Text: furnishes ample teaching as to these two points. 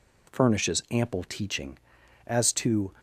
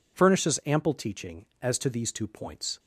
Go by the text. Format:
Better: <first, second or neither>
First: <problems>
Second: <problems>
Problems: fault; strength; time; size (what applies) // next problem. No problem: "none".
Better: second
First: stops before "these two points"; at 2.9 s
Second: none